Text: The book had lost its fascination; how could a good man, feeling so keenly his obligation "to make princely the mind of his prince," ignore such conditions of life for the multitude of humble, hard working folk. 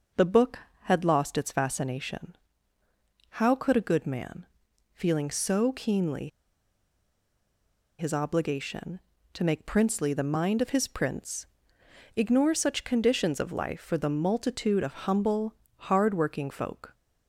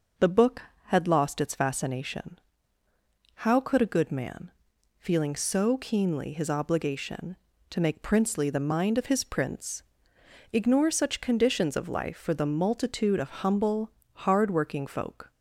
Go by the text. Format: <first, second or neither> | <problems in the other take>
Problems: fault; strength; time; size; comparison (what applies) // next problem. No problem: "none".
second | pauses between "keenly" and "his"; strong; at 6.2 s; 1.7 s long